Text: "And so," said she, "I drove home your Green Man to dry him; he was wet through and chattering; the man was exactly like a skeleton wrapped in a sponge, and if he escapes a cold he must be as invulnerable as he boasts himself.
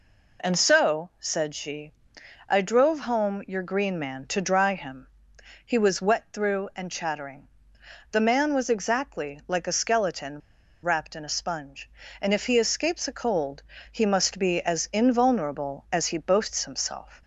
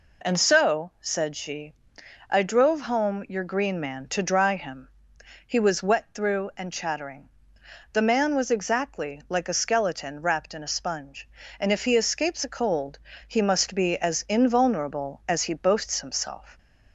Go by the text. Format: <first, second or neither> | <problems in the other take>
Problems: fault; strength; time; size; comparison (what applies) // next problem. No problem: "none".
second | pauses between "skeleton" and "wrapped"; at 10.4 s; 0.43 s long // pauses between "cold" and "he"; slight; at 13.6 s; 0.30 s long; slight in the second